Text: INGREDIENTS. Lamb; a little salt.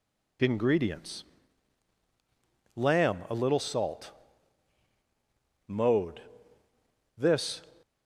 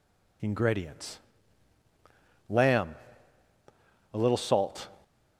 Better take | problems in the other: second | goes on to say "Mode This"; strong; from 5.6 s on; 1.9 s long

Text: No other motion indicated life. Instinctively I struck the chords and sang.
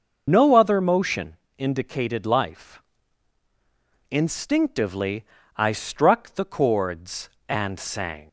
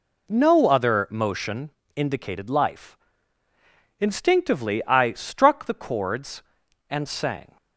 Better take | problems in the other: second | loses the start of "No"; at 0.2 s; 40 ms // pauses between "motion" and "indicated"; slight; at 1.3 s; 0.22 s long; slight in the second // pauses between "Instinctively" and "I"; slight; at 5.2 s; 0.34 s long

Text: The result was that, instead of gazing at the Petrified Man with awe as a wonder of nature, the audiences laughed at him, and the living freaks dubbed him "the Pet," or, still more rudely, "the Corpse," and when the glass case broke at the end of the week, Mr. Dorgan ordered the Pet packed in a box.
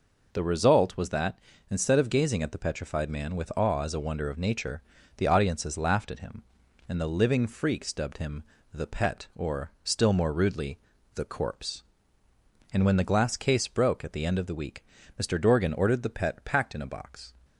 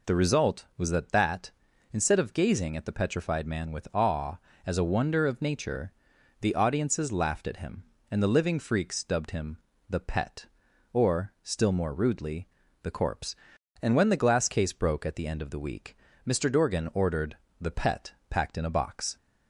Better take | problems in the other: first | says "that" twice; at 1.1 s // pauses between "him" and "the"; slight; at 9.5 s; 0.32 s long; slight in the first // pauses between "ordered" and "the"; slight; at 17.3 s; 0.20 s long // pauses between "Pet" and "packed"; slight; at 18.1 s; 0.16 s long

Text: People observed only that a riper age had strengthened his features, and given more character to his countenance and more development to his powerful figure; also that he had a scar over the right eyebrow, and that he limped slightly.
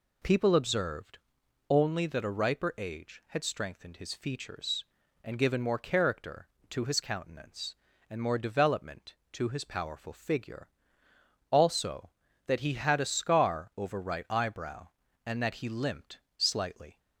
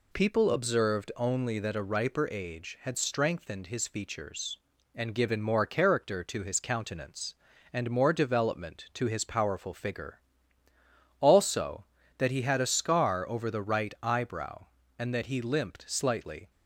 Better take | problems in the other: second | pauses between "observed" and "only"; noticeable; at 1.1 s; 0.50 s long // skips "the"; at 14.0 s // pauses between "limped" and "slightly"; slight; at 16.2 s; 0.16 s long

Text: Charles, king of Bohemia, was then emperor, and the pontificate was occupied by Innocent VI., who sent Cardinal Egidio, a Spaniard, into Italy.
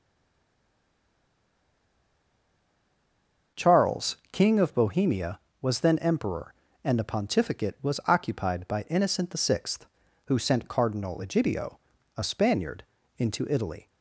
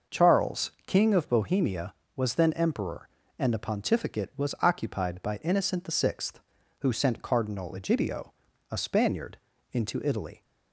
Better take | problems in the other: second | stays silent before the first word; strong; until 3.5 s; 3.5 s long

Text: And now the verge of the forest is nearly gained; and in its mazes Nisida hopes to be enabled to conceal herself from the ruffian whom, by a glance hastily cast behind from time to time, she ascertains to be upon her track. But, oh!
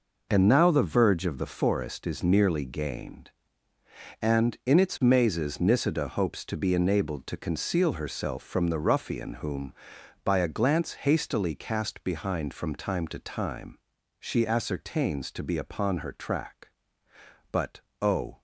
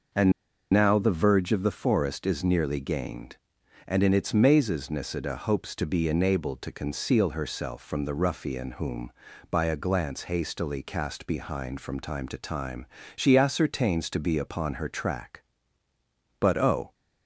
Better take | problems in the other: first | pauses between "And" and "now"; at 0.3 s; 0.39 s long

